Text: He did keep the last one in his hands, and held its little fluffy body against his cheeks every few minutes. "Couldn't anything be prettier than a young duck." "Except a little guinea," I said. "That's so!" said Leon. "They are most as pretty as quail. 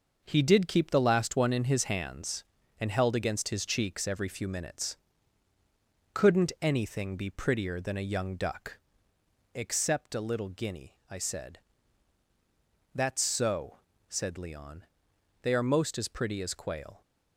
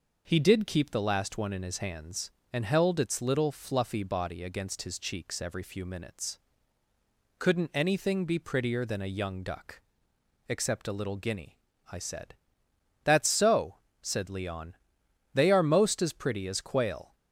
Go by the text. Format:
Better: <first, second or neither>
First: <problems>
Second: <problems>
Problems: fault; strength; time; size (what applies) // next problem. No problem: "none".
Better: second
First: starts louder than the rest; noticeable; until 1.2 s; 6 dB // skips "its little fluffy body"; at 3.1 s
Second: none